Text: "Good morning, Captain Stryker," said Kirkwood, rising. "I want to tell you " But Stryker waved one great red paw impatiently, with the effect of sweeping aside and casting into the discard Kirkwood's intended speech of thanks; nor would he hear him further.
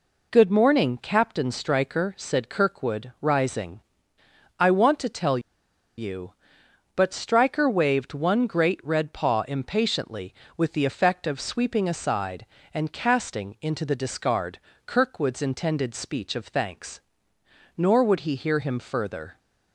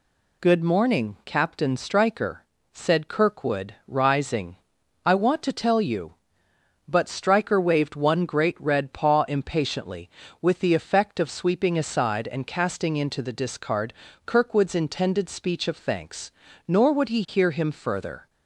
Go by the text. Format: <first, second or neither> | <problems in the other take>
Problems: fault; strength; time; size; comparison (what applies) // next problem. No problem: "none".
second | pauses between "tell" and "you"; noticeable; at 5.3 s; 0.57 s long // pauses between "discard" and "Kirkwood's"; slight; at 14.5 s; 0.26 s long; slight in the second